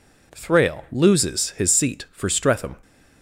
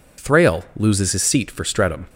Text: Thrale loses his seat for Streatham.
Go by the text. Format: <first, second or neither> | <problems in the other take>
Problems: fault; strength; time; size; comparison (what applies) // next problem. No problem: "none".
neither | none